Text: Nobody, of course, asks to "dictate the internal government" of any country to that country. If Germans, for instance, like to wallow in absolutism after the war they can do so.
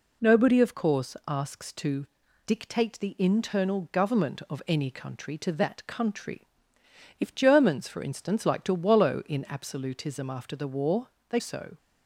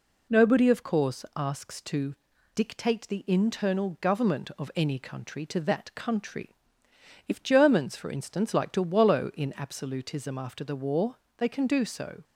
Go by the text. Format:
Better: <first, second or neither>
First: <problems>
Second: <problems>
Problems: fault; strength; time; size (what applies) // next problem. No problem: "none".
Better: second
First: pauses between "to" and "dictate"; at 2.0 s; 0.40 s long // pauses between "war" and "they"; slight; at 11.0 s; 0.22 s long // skips "can do"; at 11.3 s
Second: pauses between "to" and "dictate"; at 2.1 s; 0.40 s long // pauses between "war" and "they"; slight; at 11.1 s; 0.22 s long